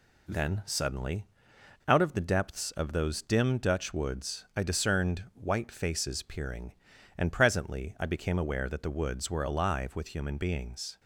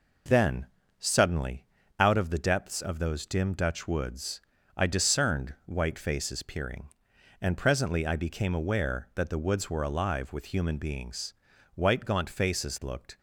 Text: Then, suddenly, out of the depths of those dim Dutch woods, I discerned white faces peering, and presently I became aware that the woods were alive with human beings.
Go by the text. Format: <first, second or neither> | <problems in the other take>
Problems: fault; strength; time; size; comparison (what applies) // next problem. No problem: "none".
first | goes on to say "White gaunt faces looked"; from 11.7 s on; 1.4 s long